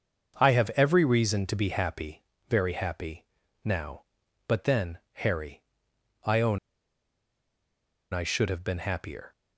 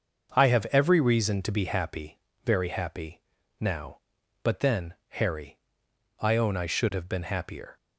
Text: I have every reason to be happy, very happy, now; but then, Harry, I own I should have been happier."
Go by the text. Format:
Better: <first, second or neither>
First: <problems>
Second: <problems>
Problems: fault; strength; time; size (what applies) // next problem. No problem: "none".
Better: second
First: starts louder than the rest; until 1.4 s; 6.5 dB // pauses between "own" and "I"; strong; at 6.5 s; 1.5 s long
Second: starts louder than the rest; until 1.3 s; 6.5 dB